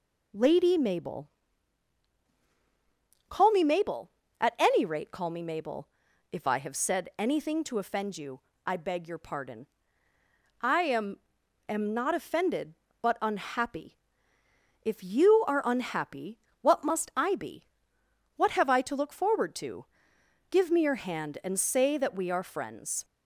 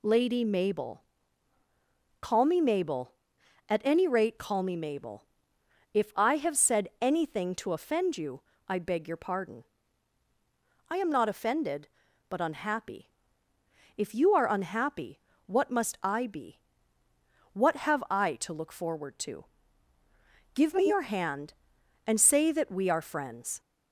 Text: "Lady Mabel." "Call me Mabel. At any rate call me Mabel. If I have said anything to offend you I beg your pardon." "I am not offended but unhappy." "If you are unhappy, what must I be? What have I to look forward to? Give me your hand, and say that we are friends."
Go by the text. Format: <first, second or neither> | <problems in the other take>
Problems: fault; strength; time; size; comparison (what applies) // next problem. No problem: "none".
second | pauses between "you" and "I"; slight; at 8.4 s; 0.26 s long; slight in the second // says "am" twice; at 11.6 s